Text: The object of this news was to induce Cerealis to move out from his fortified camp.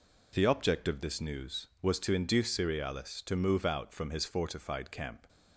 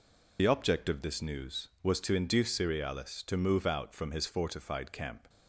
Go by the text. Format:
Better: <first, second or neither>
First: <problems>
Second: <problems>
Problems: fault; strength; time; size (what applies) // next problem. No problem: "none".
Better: first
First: none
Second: loses the start of "The"; at 0.3 s; 55 ms